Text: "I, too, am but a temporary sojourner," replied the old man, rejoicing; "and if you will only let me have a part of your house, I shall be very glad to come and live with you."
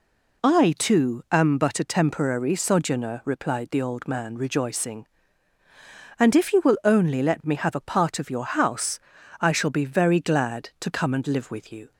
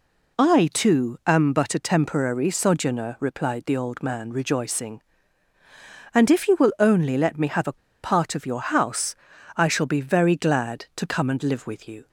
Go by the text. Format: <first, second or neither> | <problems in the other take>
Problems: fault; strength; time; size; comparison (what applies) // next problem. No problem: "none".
first | pauses between "a" and "part"; slight; at 7.7 s; 0.24 s long